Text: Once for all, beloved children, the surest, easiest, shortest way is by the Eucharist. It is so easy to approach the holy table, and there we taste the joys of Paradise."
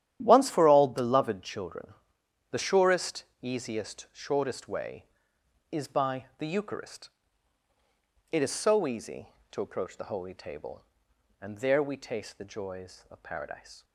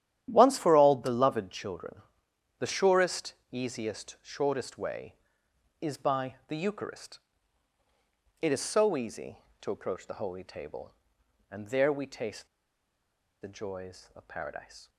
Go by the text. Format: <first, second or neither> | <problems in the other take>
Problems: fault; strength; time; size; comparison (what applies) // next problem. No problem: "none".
first | starts louder than the rest; strong; until 1.3 s; 11 dB; strong in the first // pauses between "taste" and "the"; noticeable; at 12.4 s; 0.94 s long